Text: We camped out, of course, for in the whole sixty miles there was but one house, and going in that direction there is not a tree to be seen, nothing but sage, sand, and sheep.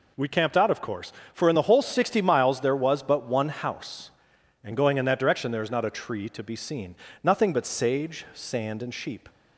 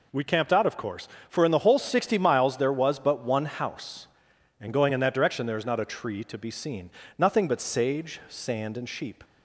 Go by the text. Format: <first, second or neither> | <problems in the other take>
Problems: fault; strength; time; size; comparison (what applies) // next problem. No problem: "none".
neither | none